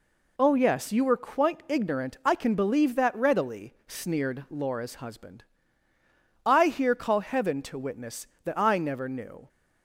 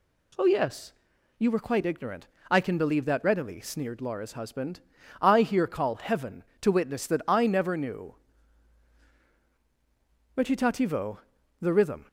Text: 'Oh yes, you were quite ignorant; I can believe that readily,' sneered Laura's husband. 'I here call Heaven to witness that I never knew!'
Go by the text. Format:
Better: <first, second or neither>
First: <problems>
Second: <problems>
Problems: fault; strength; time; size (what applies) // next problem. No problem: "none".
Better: first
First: none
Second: goes on to say "Recitativo the rhythm"; strong; from 10.3 s on; 1.7 s long